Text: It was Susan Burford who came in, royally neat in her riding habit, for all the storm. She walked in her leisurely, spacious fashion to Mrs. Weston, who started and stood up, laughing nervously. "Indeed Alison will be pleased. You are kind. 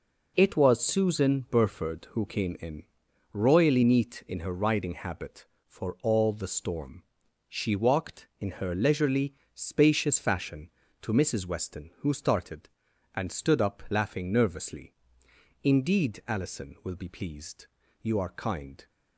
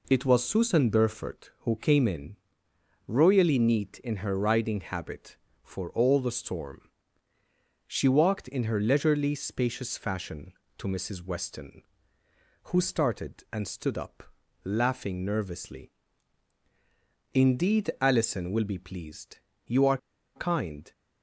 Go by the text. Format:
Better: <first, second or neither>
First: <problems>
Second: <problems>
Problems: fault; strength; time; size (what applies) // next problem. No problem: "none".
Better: first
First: none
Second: pauses between "are" and "kind"; at 19.9 s; 0.38 s long